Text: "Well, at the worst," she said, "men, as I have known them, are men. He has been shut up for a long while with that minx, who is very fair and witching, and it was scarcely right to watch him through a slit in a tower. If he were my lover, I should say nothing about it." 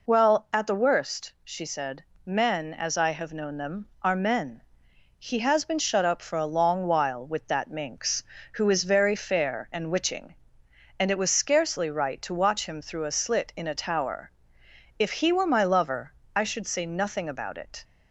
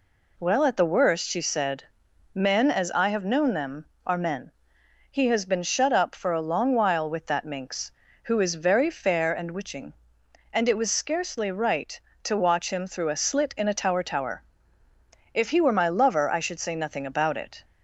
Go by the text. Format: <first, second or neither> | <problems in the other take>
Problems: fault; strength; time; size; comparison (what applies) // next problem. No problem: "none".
first | says "tower" twice; at 14.0 s